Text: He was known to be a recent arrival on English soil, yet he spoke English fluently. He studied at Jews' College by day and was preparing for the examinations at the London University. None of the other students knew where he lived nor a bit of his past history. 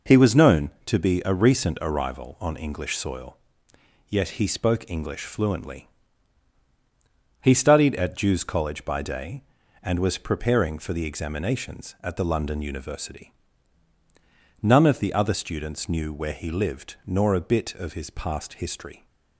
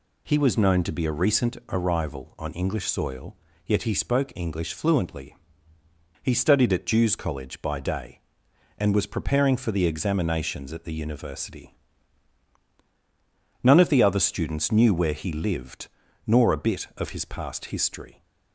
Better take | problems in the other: first | skips "London"; at 10.9 s // pauses between "lived" and "nor"; at 15.8 s; 0.38 s long

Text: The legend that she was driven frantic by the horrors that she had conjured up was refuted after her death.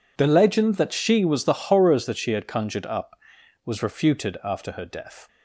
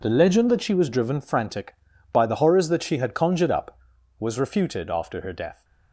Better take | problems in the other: second | skips "driven frantic by"; at 1.4 s

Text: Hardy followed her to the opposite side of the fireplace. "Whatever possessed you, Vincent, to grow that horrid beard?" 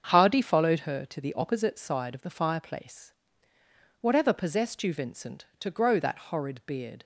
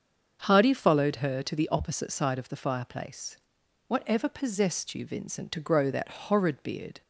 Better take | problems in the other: neither | starts louder than the rest; the same in both

